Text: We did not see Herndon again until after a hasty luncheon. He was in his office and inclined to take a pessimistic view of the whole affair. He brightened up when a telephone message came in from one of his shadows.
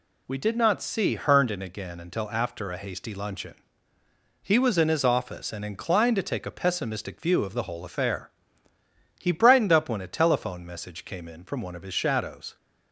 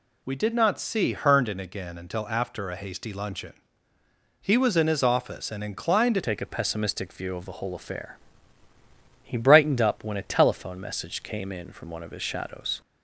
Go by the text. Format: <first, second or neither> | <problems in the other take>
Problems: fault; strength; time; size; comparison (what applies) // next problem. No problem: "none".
first | changes voice at "take"; from 6.2 s on; 6.6 s long